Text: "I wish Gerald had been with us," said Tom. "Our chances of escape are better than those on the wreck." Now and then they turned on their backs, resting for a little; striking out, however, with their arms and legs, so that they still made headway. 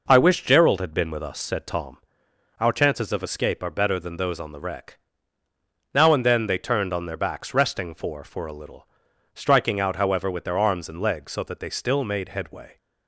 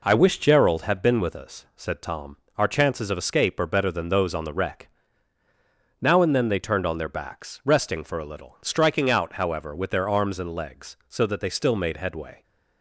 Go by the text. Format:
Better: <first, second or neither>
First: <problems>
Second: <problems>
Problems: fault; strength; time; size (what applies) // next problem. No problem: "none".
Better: second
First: says "for" twice; at 8.2 s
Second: none